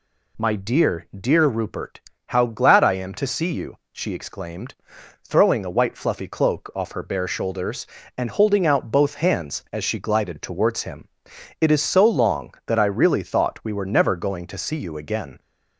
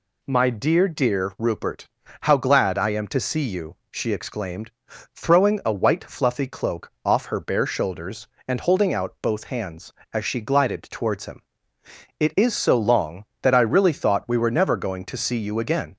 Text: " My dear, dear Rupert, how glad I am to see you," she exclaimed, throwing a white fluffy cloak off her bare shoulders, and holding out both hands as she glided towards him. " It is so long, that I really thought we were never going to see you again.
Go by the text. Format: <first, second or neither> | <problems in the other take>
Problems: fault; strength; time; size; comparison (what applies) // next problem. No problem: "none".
neither | none